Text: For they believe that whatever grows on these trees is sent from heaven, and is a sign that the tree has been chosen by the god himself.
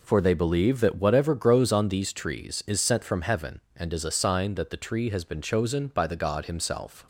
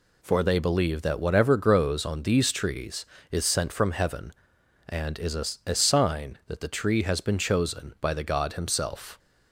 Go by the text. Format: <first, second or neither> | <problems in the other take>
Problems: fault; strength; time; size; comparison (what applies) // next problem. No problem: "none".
first | says "a" twice; at 5.6 s